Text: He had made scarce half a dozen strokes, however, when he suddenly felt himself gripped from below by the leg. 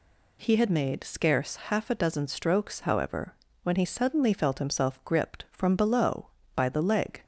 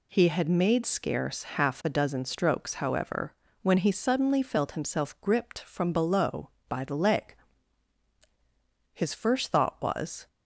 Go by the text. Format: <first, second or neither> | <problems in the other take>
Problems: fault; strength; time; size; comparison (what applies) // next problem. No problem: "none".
first | goes on to say "His first thought was"; from 8.9 s on; 1.3 s long